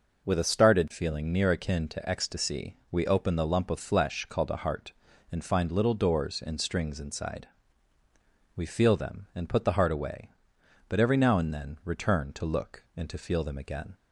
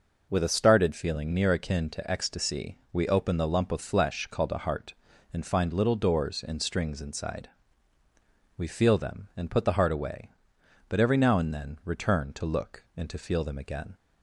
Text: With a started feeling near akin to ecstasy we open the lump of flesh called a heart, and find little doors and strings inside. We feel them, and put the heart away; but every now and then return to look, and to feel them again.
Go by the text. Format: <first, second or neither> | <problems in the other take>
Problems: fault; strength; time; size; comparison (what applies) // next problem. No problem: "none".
neither | pauses between "ecstasy" and "we"; slight; the same in both